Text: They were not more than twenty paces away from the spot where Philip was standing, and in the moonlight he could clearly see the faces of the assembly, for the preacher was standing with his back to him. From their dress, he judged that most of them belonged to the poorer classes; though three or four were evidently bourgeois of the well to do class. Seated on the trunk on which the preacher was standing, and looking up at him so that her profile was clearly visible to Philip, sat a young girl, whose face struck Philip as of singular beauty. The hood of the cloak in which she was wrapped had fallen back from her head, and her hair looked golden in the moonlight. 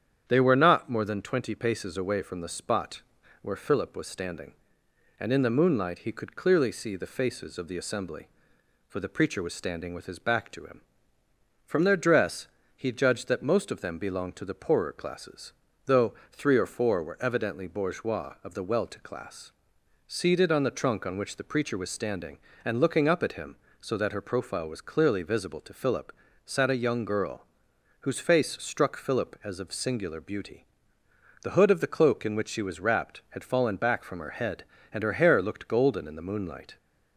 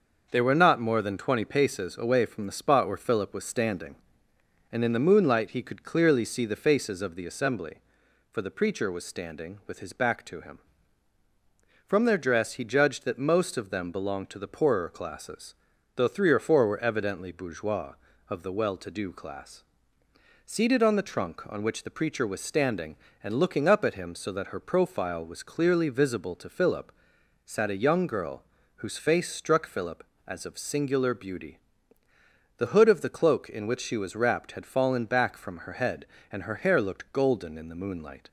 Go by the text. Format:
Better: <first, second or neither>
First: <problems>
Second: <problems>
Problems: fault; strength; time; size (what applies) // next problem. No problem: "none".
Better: second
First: starts louder than the rest; strong; until 1.2 s; 8.5 dB // pauses between "spot" and "where"; at 3.0 s; 0.40 s long // pauses between "though" and "three"; slight; at 16.1 s; 0.18 s long // skips "do"; at 18.9 s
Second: starts louder than the rest; until 1.3 s; 6 dB